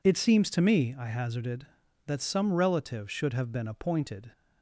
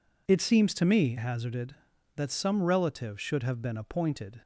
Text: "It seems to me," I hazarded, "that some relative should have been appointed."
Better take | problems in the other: first | skips "I"; at 1.1 s

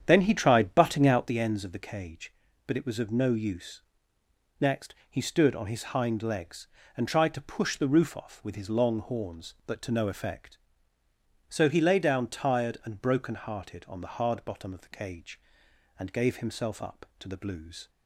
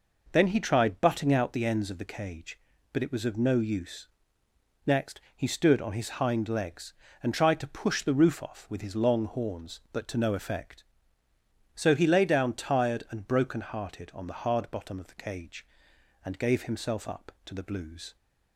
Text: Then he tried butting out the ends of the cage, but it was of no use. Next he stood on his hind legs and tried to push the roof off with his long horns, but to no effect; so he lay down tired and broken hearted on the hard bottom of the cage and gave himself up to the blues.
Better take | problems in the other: second | starts louder than the rest; strong; until 1.4 s; 8.5 dB // pauses between "Next" and "he"; slight; at 4.9 s; 0.16 s long; slight in the second

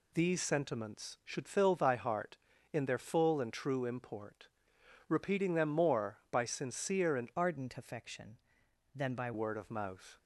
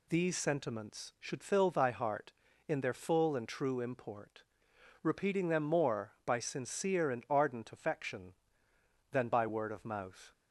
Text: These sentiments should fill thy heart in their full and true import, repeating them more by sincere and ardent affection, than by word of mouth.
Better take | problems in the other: second | changes voice from "ardent" to "by"; from 7.3 to 9.3 s; 2.0 s long

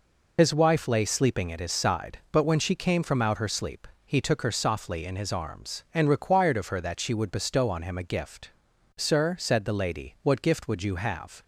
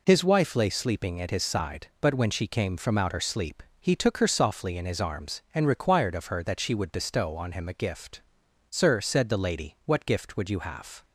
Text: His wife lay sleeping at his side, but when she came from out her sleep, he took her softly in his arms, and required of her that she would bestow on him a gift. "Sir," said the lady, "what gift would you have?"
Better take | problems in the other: second | loses the start of "His"; at 0.3 s; 55 ms

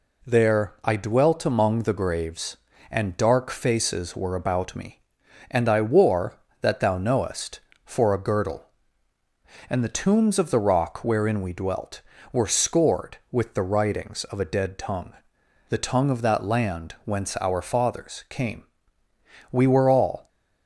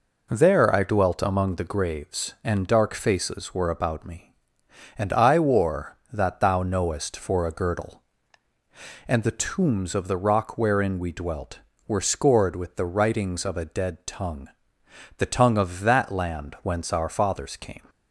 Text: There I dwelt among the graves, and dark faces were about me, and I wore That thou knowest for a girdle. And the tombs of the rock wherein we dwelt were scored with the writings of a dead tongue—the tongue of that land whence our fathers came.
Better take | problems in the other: second | goes on to say "We were all"; noticeable; from 19.5 s on; 0.78 s long

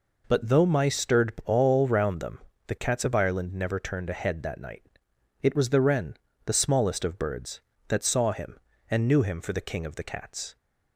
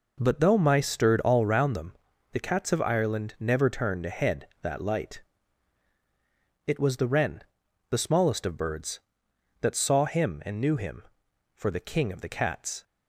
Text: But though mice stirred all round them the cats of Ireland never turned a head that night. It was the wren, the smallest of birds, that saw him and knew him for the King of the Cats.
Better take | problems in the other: first | pauses between "them" and "the"; at 1.9 s; 0.38 s long; slight in the first // says "light" for "night"; at 4.8 s

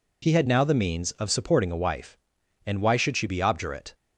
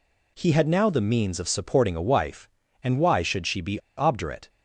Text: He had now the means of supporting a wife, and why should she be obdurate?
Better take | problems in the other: first | pauses between "be" and "obdurate"; slight; at 3.7 s; 0.19 s long

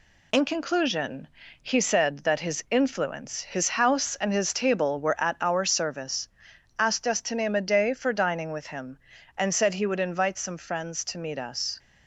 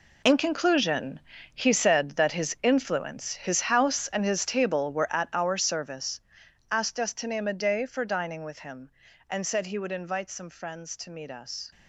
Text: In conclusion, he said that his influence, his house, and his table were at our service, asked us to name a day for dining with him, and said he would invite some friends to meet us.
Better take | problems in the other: first | gets quieter; strong; throughout; 12.5 dB

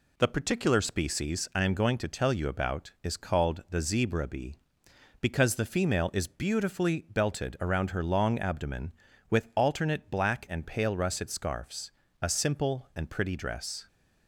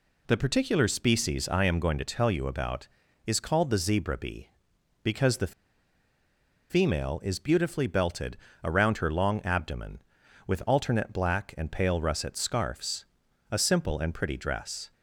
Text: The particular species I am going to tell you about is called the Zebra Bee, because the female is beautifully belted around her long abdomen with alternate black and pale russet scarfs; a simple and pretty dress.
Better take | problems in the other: first | pauses between "the" and "female"; at 5.5 s; 1.1 s long // pauses between "belted" and "around"; slight; at 8.3 s; 0.26 s long

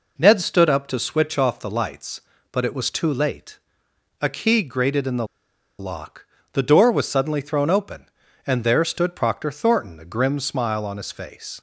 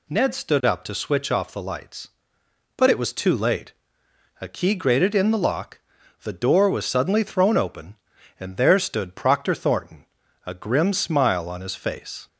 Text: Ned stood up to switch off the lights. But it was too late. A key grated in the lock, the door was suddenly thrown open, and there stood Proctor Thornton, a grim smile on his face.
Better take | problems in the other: second | pauses between "the" and "lock"; noticeable; at 5.2 s; 0.53 s long

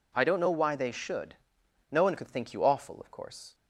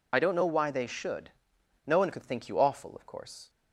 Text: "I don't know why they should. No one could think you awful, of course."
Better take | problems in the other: first | loses the start of "I"; at 0.1 s; 35 ms

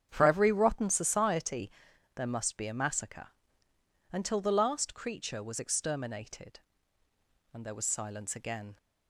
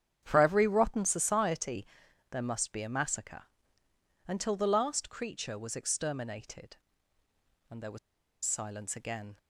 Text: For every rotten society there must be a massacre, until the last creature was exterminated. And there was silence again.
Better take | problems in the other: first | starts louder than the rest; strong; until 1.2 s; 8.5 dB; strong in the first // pauses between "society" and "there"; noticeable; at 1.8 s; 0.46 s long; noticeable in the first // pauses between "was" and "silence"; noticeable; at 7.9 s; 0.46 s long

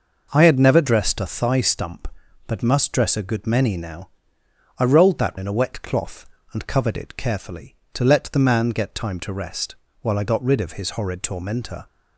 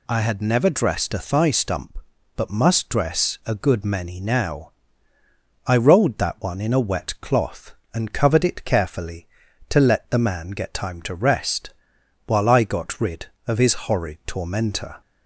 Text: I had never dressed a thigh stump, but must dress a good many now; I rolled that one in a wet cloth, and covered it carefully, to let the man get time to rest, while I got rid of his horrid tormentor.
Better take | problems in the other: second | skips "one"; at 5.3 s

